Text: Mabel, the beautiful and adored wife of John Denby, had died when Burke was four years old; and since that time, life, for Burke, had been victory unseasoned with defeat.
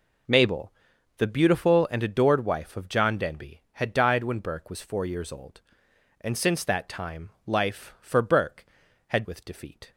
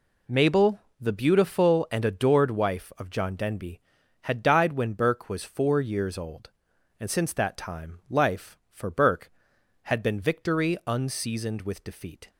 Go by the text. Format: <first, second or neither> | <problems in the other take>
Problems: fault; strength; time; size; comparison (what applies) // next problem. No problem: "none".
second | skips "been victory unseasoned"; at 9.2 s